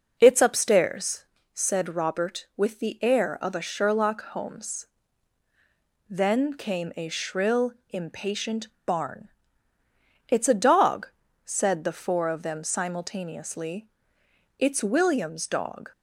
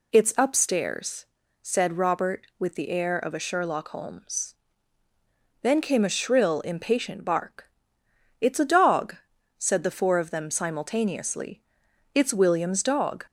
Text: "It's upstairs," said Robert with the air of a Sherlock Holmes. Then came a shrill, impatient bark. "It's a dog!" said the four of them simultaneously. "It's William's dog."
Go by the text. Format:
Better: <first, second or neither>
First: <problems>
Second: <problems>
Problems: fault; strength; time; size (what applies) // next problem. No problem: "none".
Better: second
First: says "barn" for "bark"; at 8.8 s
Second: none